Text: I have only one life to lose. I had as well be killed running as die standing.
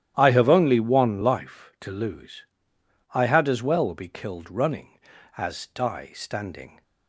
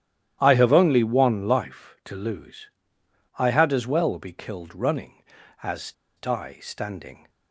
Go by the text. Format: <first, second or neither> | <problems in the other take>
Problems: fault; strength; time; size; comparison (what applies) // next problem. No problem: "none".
first | starts louder than the rest; strong; until 1.4 s; 12 dB; strong in the first // pauses between "as" and "die"; slight; at 5.9 s; 0.24 s long